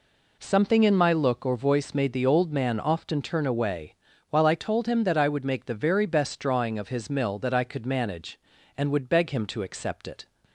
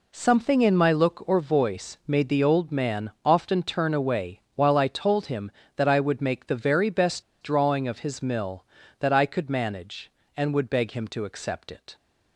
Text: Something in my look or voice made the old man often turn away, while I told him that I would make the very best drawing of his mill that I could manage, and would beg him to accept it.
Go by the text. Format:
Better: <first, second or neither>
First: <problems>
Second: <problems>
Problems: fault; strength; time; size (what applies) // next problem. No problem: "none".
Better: first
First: none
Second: pauses between "best" and "drawing"; slight; at 7.2 s; 0.18 s long